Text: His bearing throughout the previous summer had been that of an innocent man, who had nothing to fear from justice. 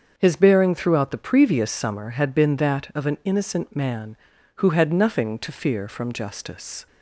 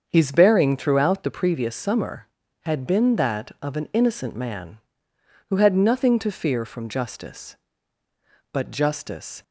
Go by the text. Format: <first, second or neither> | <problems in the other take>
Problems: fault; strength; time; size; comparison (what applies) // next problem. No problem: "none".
first | starts louder than the rest; until 1.0 s; 7 dB; also in the first // goes on to say "But justice"; noticeable; from 8.5 s on; 0.90 s long